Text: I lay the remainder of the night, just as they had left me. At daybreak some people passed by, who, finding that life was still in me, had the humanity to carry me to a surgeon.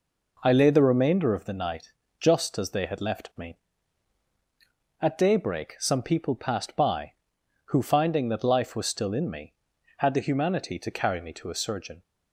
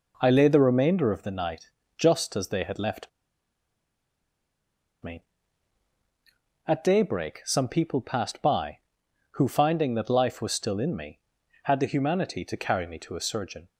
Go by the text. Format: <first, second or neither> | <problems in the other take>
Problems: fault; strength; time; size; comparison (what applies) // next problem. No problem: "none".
first | pauses between "left" and "me"; strong; at 3.0 s; 1.9 s long